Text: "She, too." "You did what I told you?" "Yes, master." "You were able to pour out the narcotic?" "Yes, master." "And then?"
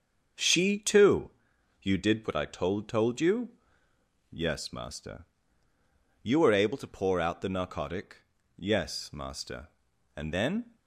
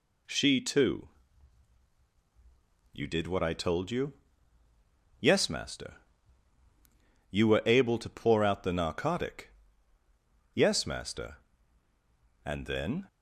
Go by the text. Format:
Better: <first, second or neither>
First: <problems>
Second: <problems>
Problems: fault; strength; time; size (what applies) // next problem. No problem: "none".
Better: second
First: starts louder than the rest; until 1.8 s; 7 dB // says "told" twice; at 2.8 s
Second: none